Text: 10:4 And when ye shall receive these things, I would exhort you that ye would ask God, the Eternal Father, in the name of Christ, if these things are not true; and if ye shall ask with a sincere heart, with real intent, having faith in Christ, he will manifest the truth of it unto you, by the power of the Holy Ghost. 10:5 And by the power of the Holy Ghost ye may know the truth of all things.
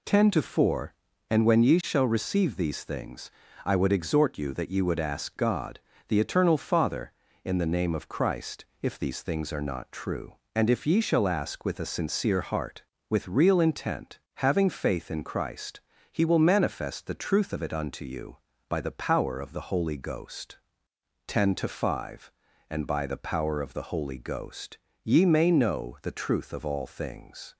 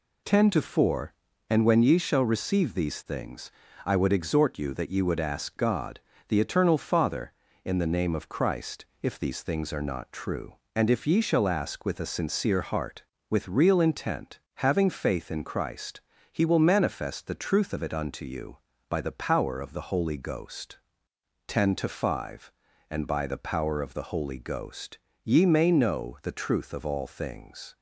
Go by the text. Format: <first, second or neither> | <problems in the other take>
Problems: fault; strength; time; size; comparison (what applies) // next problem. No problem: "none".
neither | pauses between "Ghost" and "ye"; slight; the same in both